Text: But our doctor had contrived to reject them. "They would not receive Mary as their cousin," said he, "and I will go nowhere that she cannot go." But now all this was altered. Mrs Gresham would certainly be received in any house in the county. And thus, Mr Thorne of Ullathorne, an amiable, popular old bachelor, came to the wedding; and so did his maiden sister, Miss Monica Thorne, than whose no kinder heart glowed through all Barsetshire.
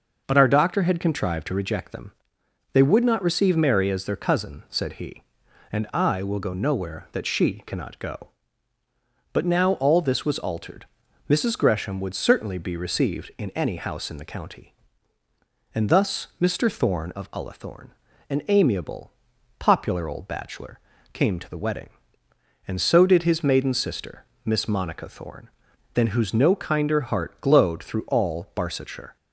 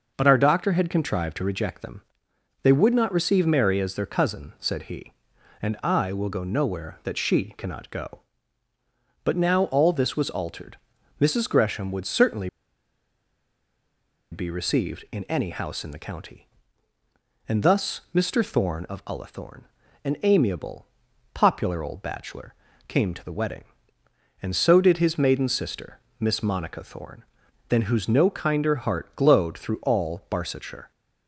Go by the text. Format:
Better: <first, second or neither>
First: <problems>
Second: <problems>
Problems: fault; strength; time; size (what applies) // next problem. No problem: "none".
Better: first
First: none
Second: pauses between "certainly" and "be"; strong; at 12.4 s; 1.8 s long